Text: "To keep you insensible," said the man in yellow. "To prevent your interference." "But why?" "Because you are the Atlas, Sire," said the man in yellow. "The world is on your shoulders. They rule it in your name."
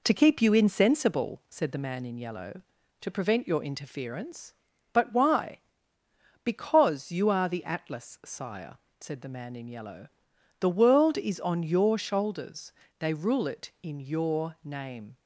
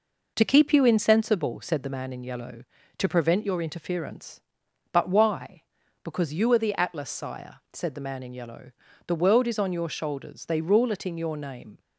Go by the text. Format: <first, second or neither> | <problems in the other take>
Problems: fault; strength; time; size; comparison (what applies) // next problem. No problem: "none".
neither | none